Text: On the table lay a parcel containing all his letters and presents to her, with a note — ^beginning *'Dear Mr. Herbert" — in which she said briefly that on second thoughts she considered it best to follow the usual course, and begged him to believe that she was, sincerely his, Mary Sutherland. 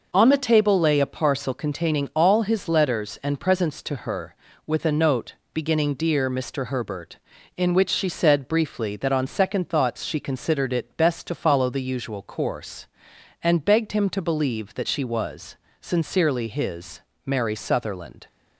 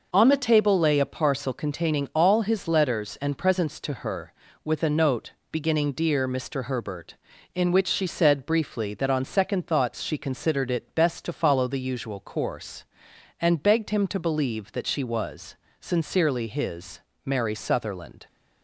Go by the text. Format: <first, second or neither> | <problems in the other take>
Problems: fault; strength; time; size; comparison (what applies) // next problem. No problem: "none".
neither | none